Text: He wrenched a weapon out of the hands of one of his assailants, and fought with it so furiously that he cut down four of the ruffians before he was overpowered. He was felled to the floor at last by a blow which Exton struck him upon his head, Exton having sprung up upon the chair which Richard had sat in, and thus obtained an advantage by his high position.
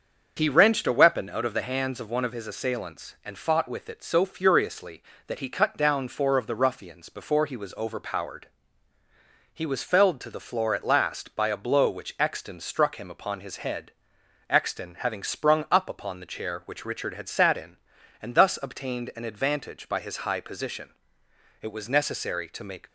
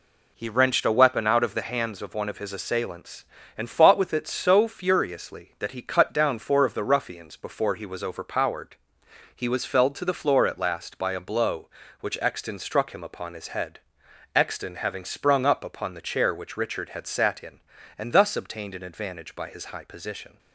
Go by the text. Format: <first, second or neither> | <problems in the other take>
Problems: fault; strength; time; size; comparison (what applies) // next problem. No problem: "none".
second | starts louder than the rest; until 1.3 s; 6.5 dB // goes on to say "It was necessary to make"; noticeable; from 21.6 s on; 1.2 s long